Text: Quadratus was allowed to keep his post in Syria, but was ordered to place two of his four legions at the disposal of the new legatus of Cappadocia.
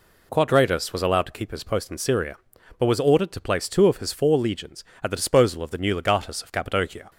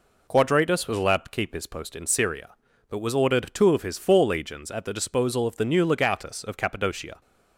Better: first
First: none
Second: skips "to place"; at 3.5 s

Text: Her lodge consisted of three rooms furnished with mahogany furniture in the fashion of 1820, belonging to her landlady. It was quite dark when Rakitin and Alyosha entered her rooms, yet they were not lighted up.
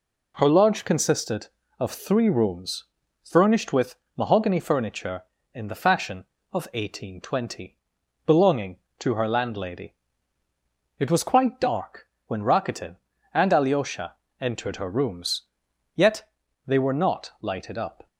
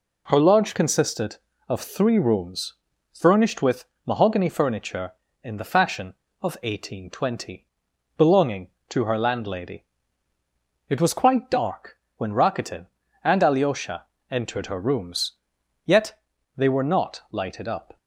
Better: neither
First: pauses between "rooms" and "furnished"; at 2.8 s; 0.40 s long // pauses between "with" and "mahogany"; slight; at 3.9 s; 0.22 s long // pauses between "dark" and "when"; slight; at 12.0 s; 0.18 s long // pauses between "Alyosha" and "entered"; slight; at 14.1 s; 0.26 s long // pauses between "yet" and "they"; at 16.2 s; 0.38 s long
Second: pauses between "rooms" and "furnished"; at 2.7 s; 0.40 s long // pauses between "with" and "mahogany"; slight; at 3.8 s; 0.22 s long // pauses between "dark" and "when"; slight; at 11.9 s; 0.18 s long // pauses between "Alyosha" and "entered"; slight; at 14.0 s; 0.26 s long // pauses between "yet" and "they"; at 16.1 s; 0.38 s long

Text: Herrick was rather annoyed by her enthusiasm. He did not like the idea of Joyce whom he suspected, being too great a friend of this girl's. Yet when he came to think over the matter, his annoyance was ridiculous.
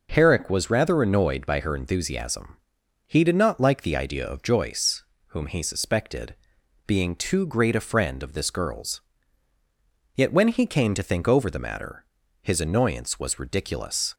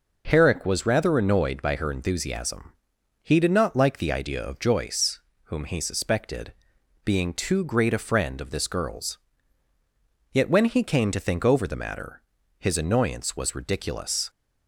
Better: neither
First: pauses between "Joyce" and "whom"; slight; at 5.0 s; 0.30 s long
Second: pauses between "Joyce" and "whom"; slight; at 5.1 s; 0.30 s long

